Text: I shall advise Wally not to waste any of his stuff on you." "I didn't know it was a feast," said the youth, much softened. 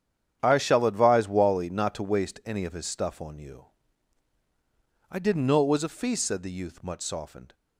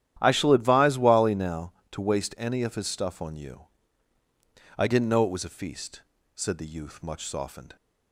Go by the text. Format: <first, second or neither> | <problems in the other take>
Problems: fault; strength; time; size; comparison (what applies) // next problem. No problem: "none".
first | starts louder than the rest; strong; until 1.2 s; 11.5 dB; strong in the first // says "now" for "not"; at 1.3 s